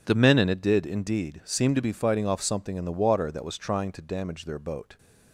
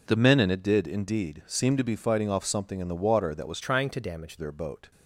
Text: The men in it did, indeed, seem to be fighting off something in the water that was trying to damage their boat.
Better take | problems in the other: first | changes voice from "trying" to "damage"; from 3.6 to 4.3 s; 0.7 s long

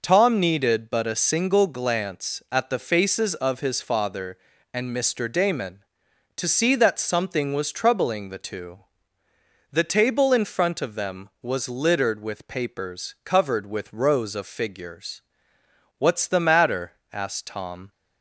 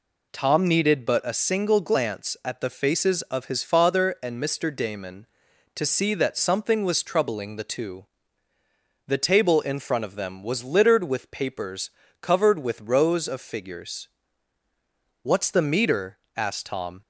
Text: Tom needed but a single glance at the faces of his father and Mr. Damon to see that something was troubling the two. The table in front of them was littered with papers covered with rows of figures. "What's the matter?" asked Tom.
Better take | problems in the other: first | pauses between "papers" and "covered"; slight; at 11.8 s; 0.32 s long // says "meter" for "matter"; at 15.6 s

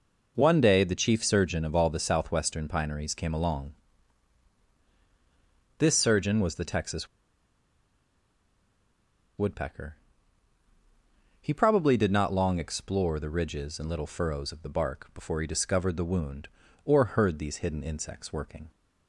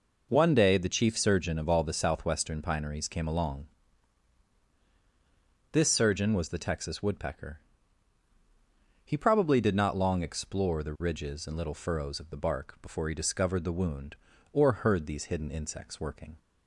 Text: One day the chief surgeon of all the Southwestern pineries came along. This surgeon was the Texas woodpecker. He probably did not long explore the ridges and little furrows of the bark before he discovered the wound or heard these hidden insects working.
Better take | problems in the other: second | pauses between "Texas" and "woodpecker"; strong; at 7.0 s; 2.3 s long

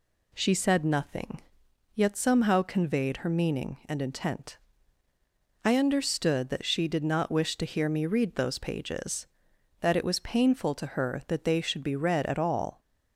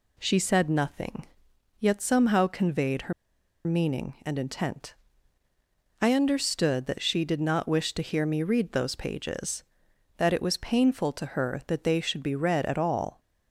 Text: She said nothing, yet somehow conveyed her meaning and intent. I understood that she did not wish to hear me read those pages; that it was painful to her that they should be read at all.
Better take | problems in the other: first | pauses between "her" and "meaning"; noticeable; at 3.1 s; 0.53 s long

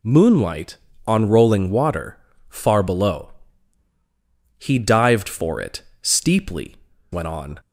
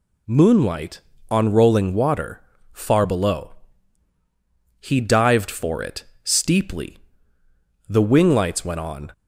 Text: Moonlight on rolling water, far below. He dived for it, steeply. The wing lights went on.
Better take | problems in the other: second | skips "The wing lights"; at 6.9 s

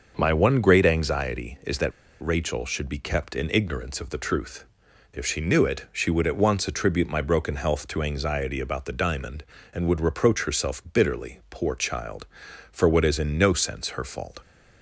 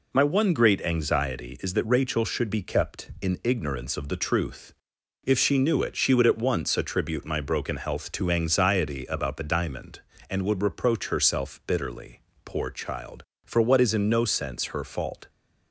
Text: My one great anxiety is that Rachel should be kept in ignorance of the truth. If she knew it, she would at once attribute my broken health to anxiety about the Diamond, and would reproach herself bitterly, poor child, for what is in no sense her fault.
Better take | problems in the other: second | starts louder than the rest; until 1.1 s; 6 dB // pauses between "that" and "Rachel"; slight; at 1.9 s; 0.30 s long

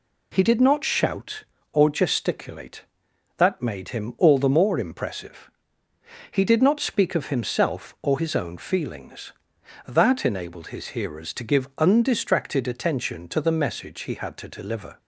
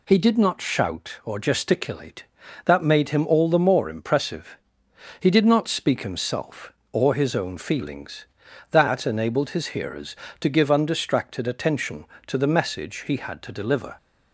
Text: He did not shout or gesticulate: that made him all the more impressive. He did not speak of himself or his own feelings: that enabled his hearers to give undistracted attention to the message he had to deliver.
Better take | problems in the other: first | skips "of"; at 6.0 s

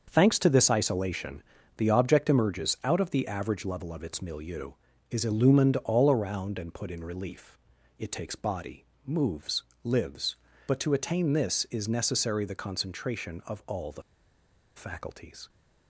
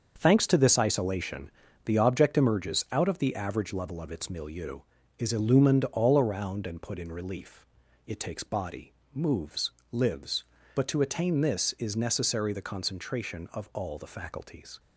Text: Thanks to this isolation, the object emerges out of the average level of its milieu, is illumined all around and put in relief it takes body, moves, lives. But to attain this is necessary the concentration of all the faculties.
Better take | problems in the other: second | starts louder than the rest; until 1.1 s; 6.5 dB; also in the second // pauses between "relief" and "it"; at 7.5 s; 0.40 s long; also in the second // pauses between "the" and "faculties"; noticeable; at 14.0 s; 0.74 s long

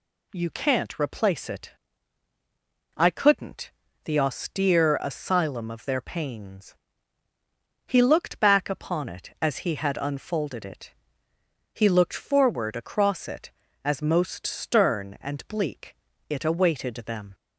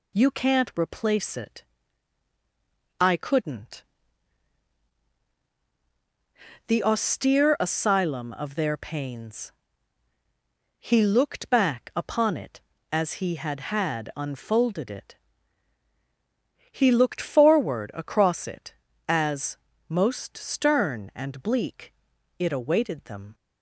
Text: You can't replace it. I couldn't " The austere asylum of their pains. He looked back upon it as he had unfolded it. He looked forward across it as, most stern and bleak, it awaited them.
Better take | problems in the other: first | says "had" twice; at 13.7 s

